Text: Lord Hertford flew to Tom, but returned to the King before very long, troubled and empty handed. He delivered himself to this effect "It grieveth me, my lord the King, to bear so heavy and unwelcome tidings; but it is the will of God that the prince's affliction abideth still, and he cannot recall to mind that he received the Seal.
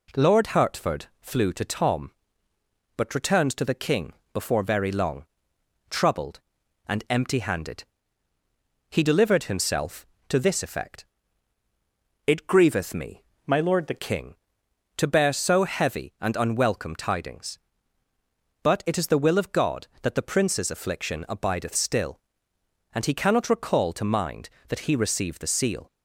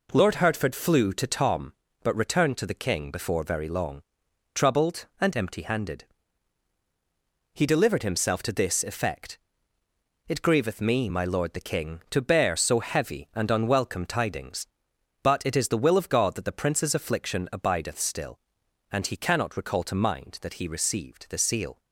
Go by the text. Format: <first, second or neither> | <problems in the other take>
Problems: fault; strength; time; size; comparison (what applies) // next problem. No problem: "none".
second | pauses between "Hertford" and "flew"; slight; at 1.0 s; 0.16 s long // pauses between "King" and "before"; slight; at 4.1 s; 0.20 s long // pauses between "effect" and "It"; at 11.0 s; 1.2 s long; noticeable in the second // changes voice from "my" to "the"; from 13.4 to 13.9 s; 0.5 s long